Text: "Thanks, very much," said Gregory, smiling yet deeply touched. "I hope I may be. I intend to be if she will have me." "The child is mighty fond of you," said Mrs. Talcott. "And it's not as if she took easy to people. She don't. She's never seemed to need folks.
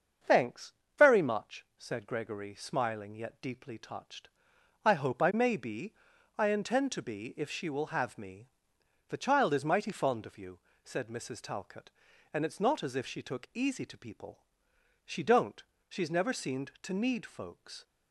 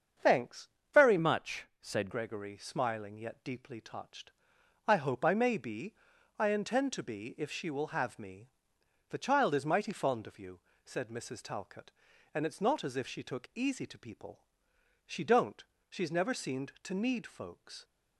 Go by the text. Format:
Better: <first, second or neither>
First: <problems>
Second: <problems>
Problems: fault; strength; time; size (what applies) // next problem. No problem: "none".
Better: first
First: starts louder than the rest; until 1.5 s; 7 dB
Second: starts louder than the rest; strong; until 1.4 s; 7 dB // changes voice from "much" to "said"; from 1.1 to 2.0 s; 0.9 s long